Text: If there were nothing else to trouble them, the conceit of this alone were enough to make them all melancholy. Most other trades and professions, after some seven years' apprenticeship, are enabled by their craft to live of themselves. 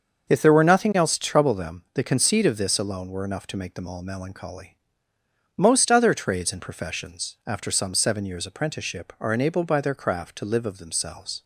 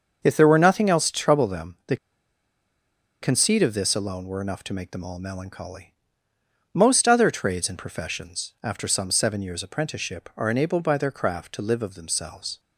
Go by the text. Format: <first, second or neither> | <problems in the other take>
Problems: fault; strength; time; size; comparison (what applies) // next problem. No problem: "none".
first | starts louder than the rest; until 1.2 s; 6.5 dB; also in the first // pauses between "the" and "conceit"; strong; at 1.9 s; 1.2 s long